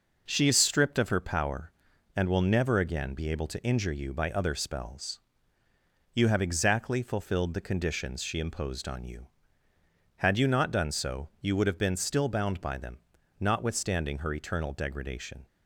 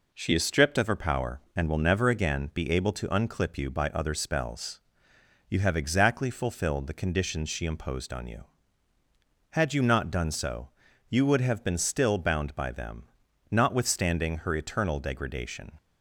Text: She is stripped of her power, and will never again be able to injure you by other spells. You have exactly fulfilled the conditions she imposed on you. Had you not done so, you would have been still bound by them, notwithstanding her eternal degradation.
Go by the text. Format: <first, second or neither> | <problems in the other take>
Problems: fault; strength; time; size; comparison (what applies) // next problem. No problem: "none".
first | says "unclip" for "injure"; at 3.0 s